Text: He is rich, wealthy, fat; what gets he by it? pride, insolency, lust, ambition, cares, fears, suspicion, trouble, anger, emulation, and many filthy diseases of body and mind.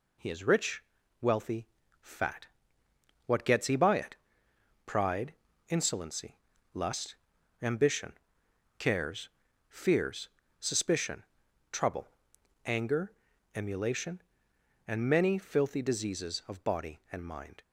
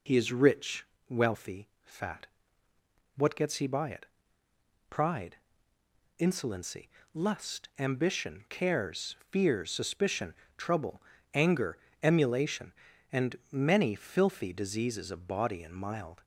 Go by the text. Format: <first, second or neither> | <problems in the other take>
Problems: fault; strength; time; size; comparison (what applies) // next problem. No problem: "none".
first | pauses between "and" and "many"; slight; at 13.3 s; 0.16 s long // says "mild" for "mind"; at 15.7 s